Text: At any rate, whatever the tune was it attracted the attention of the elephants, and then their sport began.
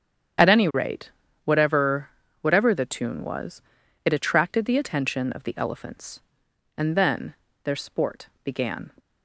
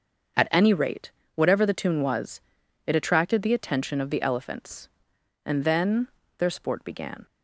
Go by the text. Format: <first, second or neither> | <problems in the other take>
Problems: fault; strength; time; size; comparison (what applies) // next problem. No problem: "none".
second | starts louder than the rest; strong; until 1.7 s; 8.5 dB; also in the second // says "whatever" twice; at 2.4 s // pauses between "was" and "it"; at 3.6 s; 0.44 s long; also in the second // pauses between "then" and "their"; slight; at 7.3 s; 0.28 s long; slight in the second // pauses between "sport" and "began"; slight; at 8.2 s; 0.16 s long